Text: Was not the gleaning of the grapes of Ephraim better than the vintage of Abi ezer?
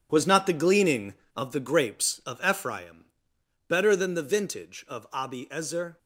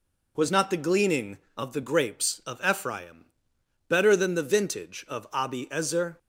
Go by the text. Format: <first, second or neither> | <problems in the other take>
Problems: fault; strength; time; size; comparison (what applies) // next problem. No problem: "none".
second | gets quieter; strong; throughout; 10.5 dB // pauses between "Ephraim" and "better"; noticeable; at 3.0 s; 0.62 s long; noticeable in the second